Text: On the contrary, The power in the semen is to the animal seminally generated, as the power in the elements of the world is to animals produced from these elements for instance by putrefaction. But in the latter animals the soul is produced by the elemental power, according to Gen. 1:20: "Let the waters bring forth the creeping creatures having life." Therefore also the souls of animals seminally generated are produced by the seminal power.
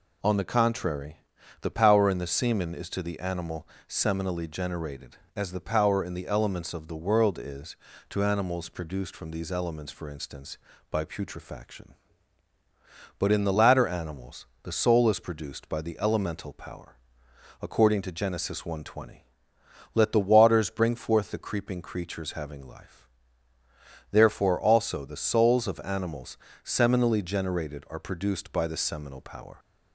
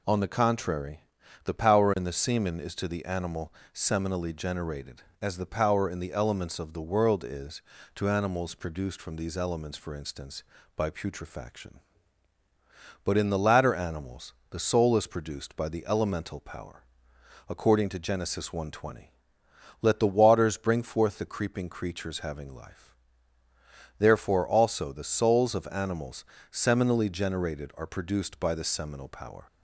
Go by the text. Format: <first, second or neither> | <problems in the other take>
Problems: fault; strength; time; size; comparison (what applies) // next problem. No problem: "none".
neither | pauses between "animal" and "seminally"; slight; the same in both // pauses between "animals" and "the"; slight; the same in both // pauses between "animals" and "seminally"; slight; the same in both